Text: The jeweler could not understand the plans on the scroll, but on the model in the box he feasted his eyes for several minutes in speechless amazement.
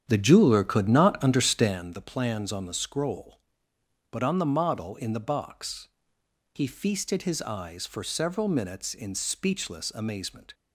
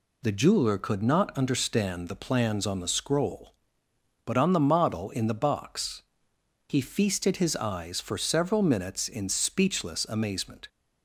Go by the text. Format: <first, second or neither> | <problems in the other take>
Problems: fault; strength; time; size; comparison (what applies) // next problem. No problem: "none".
second | starts louder than the rest; strong; until 1.8 s; 9 dB // pauses between "box" and "he"; noticeable; at 5.8 s; 0.66 s long; noticeable in the second